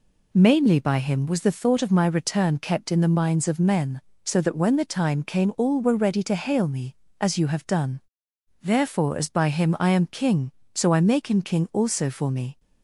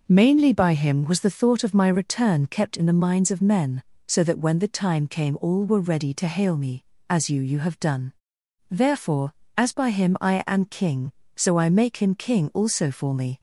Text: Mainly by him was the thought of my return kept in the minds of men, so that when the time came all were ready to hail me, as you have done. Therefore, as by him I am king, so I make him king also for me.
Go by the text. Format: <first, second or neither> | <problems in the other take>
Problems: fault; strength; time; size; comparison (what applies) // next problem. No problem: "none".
first | says "you" twice; at 7.3 s